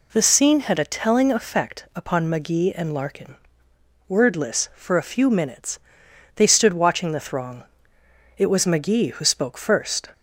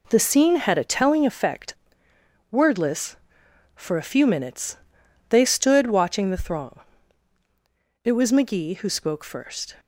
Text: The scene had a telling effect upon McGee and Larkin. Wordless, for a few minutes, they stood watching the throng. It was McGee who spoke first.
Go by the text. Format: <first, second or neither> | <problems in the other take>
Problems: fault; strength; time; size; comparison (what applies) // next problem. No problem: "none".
first | skips "upon McGee and Larkin"; at 2.1 s